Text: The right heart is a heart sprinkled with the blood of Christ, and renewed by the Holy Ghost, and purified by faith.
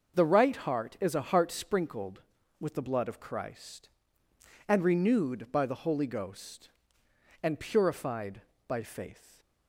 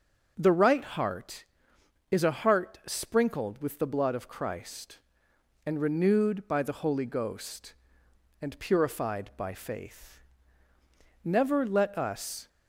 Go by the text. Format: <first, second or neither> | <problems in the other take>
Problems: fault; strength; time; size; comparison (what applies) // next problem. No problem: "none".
first | starts louder than the rest; until 1.3 s; 6 dB; also in the first // goes on to say "Never let us"; noticeable; from 11.2 s on; 1.2 s long